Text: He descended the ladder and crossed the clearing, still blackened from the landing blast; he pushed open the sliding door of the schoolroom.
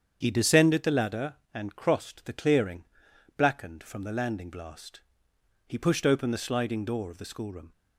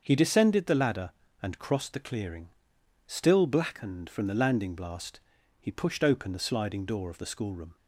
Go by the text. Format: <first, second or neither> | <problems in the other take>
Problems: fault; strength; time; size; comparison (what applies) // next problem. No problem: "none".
second | starts louder than the rest; strong; until 1.2 s; 8 dB; also in the second // skips "still"; at 3.1 s